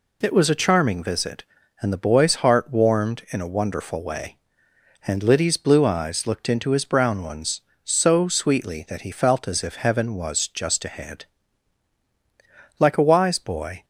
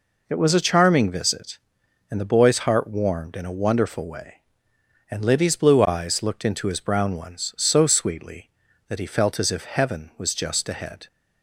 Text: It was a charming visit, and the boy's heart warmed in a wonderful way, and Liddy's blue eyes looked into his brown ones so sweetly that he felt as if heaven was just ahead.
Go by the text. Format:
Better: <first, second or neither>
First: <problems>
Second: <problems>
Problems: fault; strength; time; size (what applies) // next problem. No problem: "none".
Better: second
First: goes on to say "Like a wise boy"; noticeable; from 12.7 s on; 1.0 s long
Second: none